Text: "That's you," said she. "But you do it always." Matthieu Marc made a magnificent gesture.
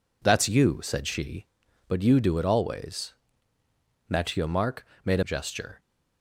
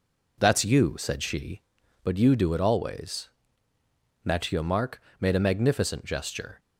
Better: second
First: pauses between "Marc" and "made"; slight; at 4.8 s; 0.20 s long // skips "magnificent"; at 5.2 s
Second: pauses between "Marc" and "made"; slight; at 5.0 s; 0.20 s long

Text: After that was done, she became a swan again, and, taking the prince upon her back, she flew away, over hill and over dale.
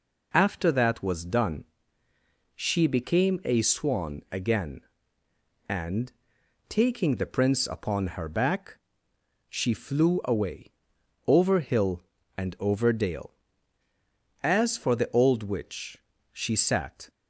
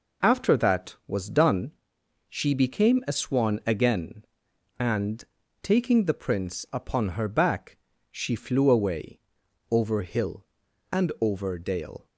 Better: second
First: goes on to say "As for the old witch she sat"; strong; from 14.4 s on; 2.6 s long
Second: none

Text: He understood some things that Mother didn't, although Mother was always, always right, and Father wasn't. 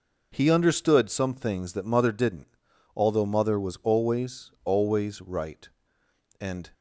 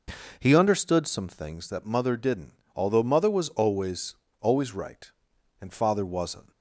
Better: second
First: stops before "Father wasn't"; at 6.7 s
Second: none

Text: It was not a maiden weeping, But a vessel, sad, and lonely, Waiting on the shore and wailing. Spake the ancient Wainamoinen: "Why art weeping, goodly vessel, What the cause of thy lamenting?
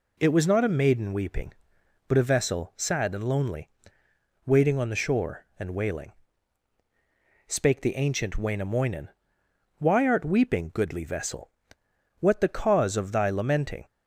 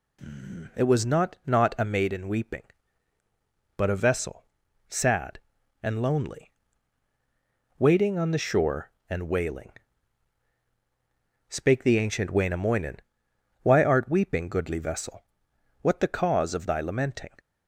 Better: first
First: none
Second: says "not" twice; at 1.4 s

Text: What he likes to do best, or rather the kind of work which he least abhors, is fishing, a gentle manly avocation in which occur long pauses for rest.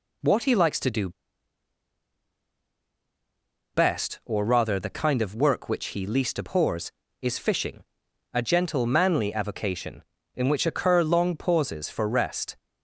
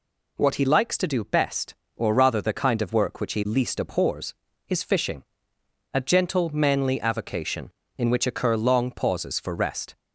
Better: second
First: pauses between "do" and "best"; strong; at 1.1 s; 2.6 s long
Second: none

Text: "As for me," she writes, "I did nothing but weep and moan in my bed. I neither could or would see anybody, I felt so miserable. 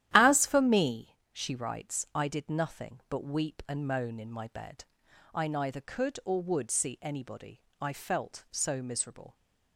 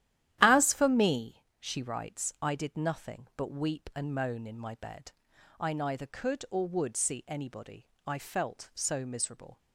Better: neither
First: starts louder than the rest; strong; until 1.1 s; 12 dB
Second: starts louder than the rest; strong; until 1.4 s; 12 dB

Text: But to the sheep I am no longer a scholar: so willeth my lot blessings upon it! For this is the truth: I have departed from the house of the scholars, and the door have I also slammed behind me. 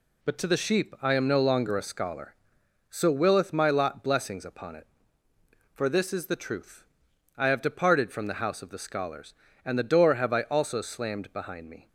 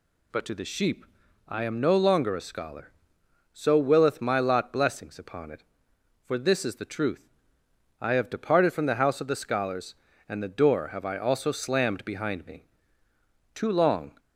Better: first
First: none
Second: pauses between "sheep" and "I"; at 1.0 s; 0.42 s long // goes on to say "Too long"; noticeable; from 13.5 s on; 0.66 s long

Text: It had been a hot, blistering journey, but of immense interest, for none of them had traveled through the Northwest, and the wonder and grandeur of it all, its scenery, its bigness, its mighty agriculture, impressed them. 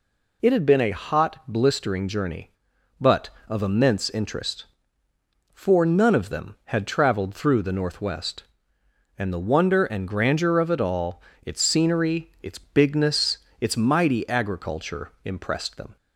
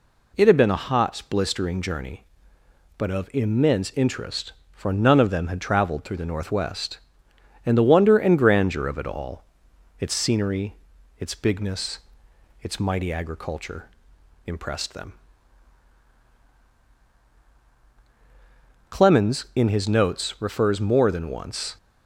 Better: first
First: none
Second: goes on to say "Clemens in his notes refers more than once"; strong; from 18.8 s on; 2.8 s long

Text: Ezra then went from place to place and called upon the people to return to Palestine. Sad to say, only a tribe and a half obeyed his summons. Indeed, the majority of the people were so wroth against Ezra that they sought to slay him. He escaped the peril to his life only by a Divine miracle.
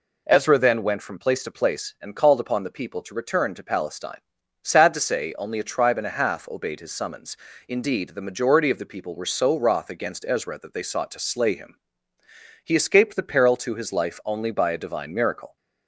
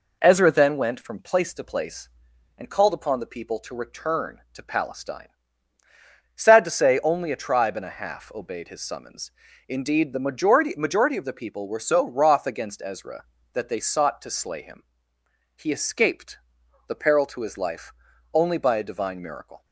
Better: first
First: none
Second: says "majority" twice; at 10.7 s // pauses between "escaped" and "the"; noticeable; at 16.3 s; 0.50 s long // pauses between "life" and "only"; at 17.9 s; 0.40 s long

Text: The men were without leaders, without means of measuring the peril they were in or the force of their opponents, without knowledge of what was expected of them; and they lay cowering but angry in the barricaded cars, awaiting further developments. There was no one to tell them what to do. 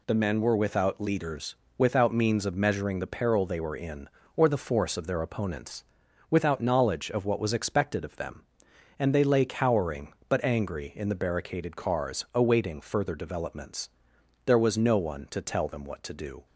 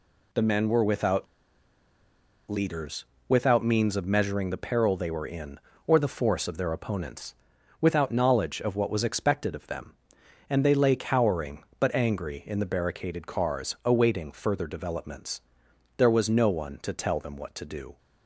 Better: first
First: none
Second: pauses between "without" and "leaders"; at 1.2 s; 1.2 s long

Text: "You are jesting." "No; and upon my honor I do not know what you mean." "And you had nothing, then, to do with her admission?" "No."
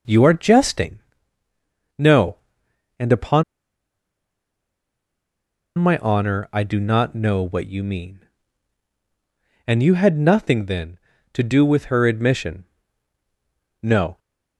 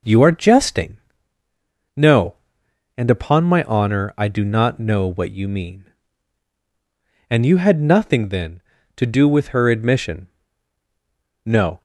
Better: second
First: pauses between "upon" and "my"; strong; at 3.4 s; 2.3 s long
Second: none

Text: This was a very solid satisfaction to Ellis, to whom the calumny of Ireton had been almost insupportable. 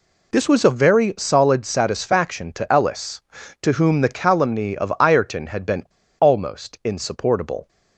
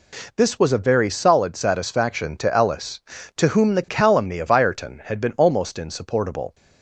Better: second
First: pauses between "been" and "almost"; slight; at 5.8 s; 0.35 s long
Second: none

